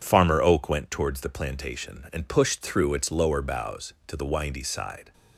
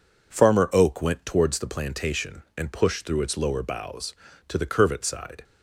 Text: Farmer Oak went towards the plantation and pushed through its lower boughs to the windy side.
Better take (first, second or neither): first